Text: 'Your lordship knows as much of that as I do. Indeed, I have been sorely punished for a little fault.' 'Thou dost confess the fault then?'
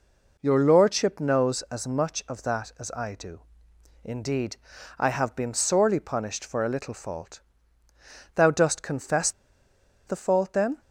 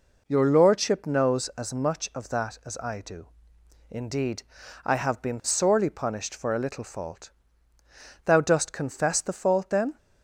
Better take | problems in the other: second | pauses between "confess" and "the"; noticeable; at 9.3 s; 0.75 s long

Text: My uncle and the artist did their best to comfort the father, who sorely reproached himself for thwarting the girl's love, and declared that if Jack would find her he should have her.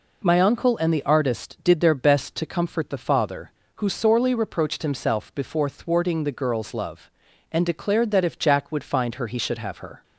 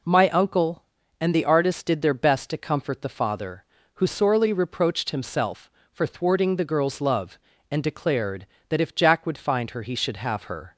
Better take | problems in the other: second | says "before" for "for"; at 5.3 s

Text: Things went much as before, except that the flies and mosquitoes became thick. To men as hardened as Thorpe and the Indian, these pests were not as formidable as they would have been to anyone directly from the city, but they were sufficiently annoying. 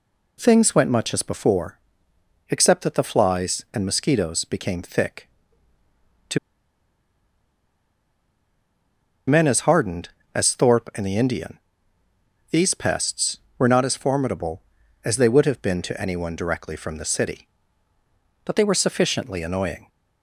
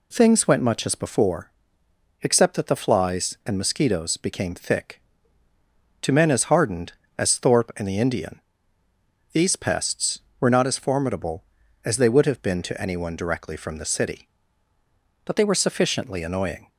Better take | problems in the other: second | pauses between "To" and "men"; strong; at 6.3 s; 2.8 s long

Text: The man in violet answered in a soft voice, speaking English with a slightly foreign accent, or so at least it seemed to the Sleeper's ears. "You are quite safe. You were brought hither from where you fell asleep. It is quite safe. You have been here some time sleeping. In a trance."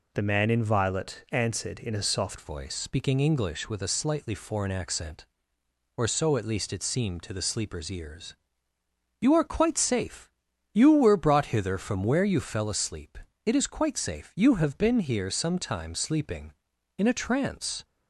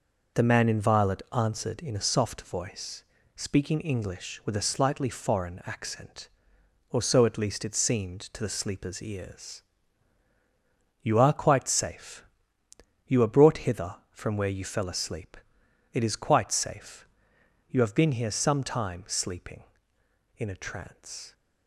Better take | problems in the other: second | changes voice at "voice"; from 2.3 s on; 15.5 s long

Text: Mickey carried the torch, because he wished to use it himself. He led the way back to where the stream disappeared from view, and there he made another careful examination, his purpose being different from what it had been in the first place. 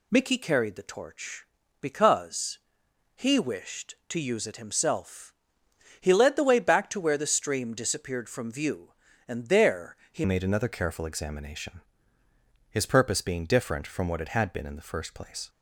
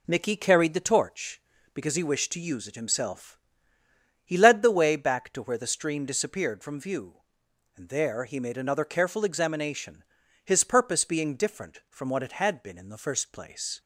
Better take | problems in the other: second | pauses between "because" and "he"; noticeable; at 2.5 s; 0.58 s long // pauses between "there" and "he"; slight; at 9.9 s; 0.16 s long // changes voice at "made"; from 10.2 s on; 5.2 s long

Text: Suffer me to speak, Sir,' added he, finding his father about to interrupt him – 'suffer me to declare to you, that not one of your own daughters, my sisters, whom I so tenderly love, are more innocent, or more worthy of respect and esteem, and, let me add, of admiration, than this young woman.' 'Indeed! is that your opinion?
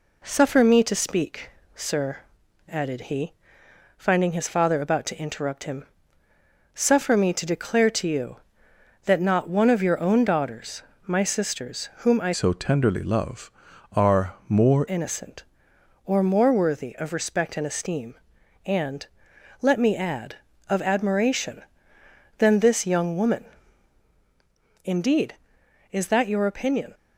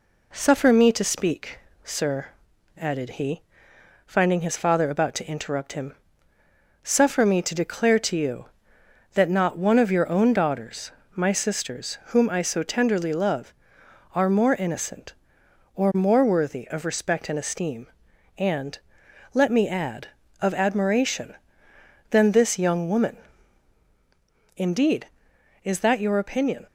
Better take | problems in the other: second | changes voice from "so" to "more"; from 12.3 to 14.8 s; 2.5 s long

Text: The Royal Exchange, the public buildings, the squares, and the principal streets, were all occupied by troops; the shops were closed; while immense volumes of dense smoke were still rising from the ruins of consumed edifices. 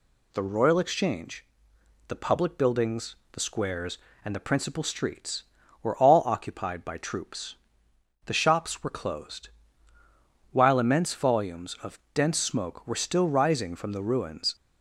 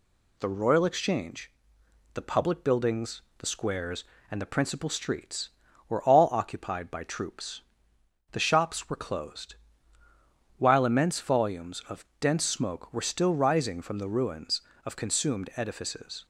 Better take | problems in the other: second | stops before "of consumed edifices"; at 14.5 s

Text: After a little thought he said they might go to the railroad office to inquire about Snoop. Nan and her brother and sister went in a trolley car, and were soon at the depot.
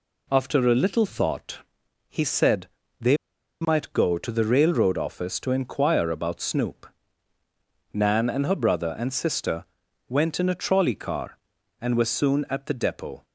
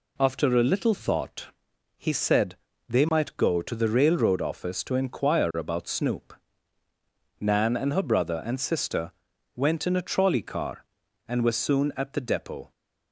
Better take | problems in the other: second | pauses between "thought" and "he"; noticeable; at 1.5 s; 0.50 s long; noticeable in the second // pauses between "said" and "they"; slight; at 2.6 s; 0.32 s long; slight in the second // pauses between "they" and "might"; at 3.1 s; 0.45 s long // pauses between "sister" and "went"; at 9.6 s; 0.44 s long; also in the second

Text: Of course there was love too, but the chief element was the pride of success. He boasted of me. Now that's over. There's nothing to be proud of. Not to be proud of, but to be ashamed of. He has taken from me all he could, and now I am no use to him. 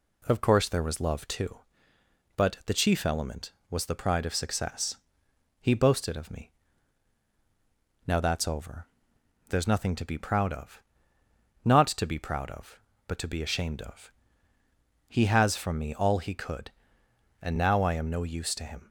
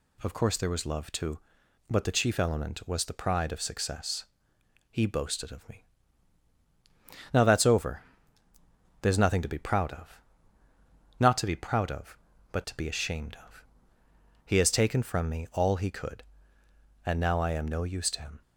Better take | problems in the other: second | skips "taken"; at 15.5 s

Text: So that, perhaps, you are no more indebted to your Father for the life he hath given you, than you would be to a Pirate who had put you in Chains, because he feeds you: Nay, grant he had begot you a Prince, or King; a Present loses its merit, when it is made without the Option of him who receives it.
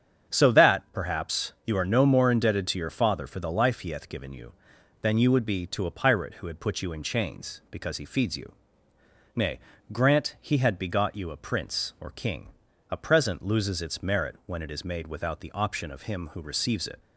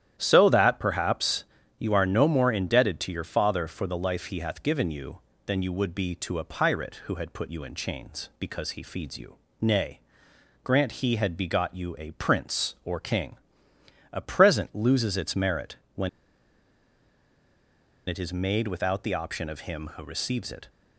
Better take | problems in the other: first | starts louder than the rest; strong; until 1.1 s; 11 dB; strong in the first // pauses between "when" and "it"; strong; at 16.0 s; 1.9 s long

